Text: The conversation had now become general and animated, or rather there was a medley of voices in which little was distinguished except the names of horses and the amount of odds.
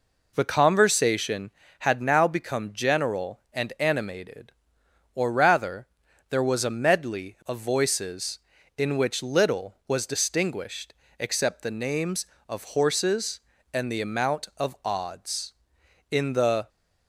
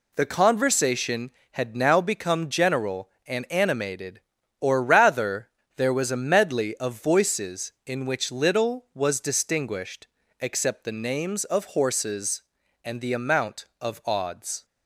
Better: second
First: pauses between "rather" and "there"; at 5.8 s; 0.44 s long // pauses between "distinguished" and "except"; slight; at 10.9 s; 0.28 s long // goes on to say "In the"; from 16.1 s on; 0.58 s long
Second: pauses between "rather" and "there"; slight; at 5.4 s; 0.28 s long // pauses between "distinguished" and "except"; slight; at 10.0 s; 0.32 s long

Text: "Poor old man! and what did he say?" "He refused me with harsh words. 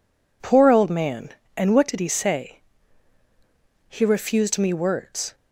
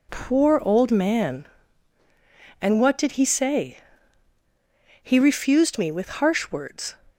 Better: second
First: skips "with harsh"; at 4.7 s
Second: none

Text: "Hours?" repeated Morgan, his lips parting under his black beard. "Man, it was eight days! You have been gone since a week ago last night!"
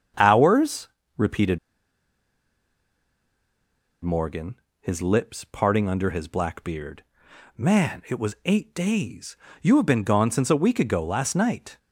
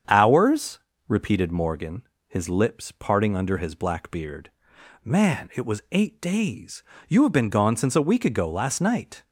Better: second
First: starts louder than the rest; strong; until 1.4 s; 7.5 dB // pauses between "repeated" and "Morgan"; strong; at 1.5 s; 2.4 s long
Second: starts louder than the rest; strong; until 1.3 s; 7.5 dB

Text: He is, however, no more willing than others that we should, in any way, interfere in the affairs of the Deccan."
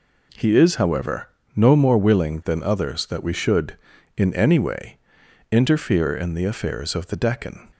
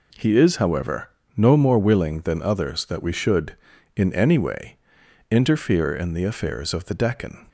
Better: neither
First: none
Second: none

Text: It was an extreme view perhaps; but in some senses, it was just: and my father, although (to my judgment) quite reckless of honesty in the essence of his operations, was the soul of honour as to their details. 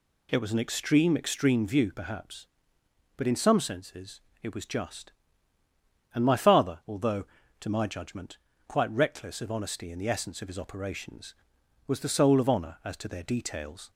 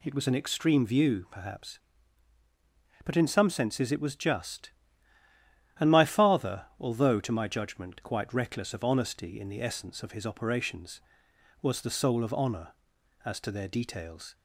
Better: second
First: says "extreme" twice; at 1.1 s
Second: none

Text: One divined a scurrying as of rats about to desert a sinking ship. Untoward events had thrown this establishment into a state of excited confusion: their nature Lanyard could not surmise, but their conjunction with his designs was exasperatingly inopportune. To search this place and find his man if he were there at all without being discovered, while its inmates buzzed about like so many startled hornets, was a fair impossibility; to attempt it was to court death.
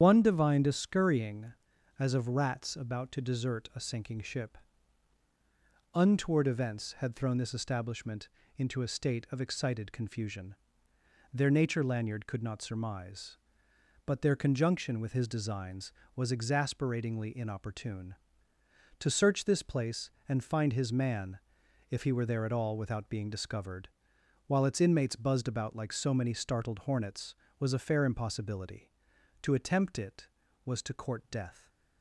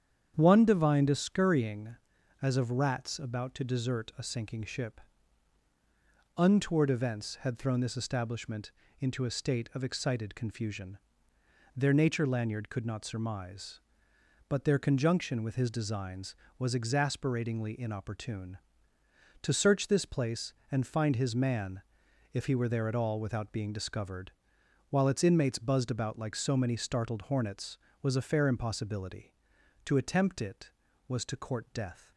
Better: second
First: loses the start of "One"; at 0.0 s; 85 ms // starts louder than the rest; strong; until 1.0 s; 8.5 dB // pauses between "establishment" and "into"; slight; at 8.2 s; 0.26 s long // pauses between "man" and "if"; noticeable; at 21.3 s; 0.52 s long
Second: starts louder than the rest; strong; until 1.3 s; 8.5 dB // pauses between "establishment" and "into"; slight; at 8.7 s; 0.26 s long // pauses between "man" and "if"; noticeable; at 21.8 s; 0.52 s long

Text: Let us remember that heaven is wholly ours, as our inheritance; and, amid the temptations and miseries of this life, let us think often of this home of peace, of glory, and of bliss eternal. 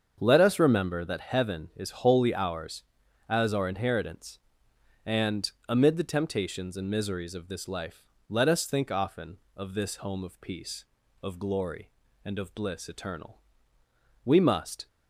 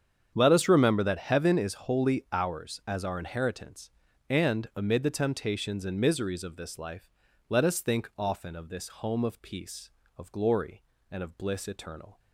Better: second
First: starts louder than the rest; until 1.2 s; 7 dB // goes on to say "We must"; noticeable; from 14.2 s on; 0.62 s long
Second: starts louder than the rest; strong; until 1.3 s; 8 dB

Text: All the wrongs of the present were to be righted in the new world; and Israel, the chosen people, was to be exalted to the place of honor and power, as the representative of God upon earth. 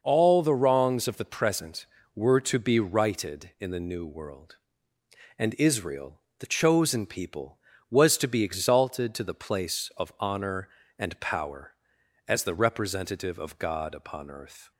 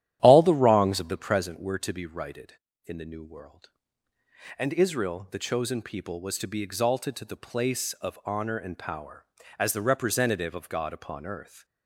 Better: first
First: none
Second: starts louder than the rest; strong; until 1.5 s; 12.5 dB

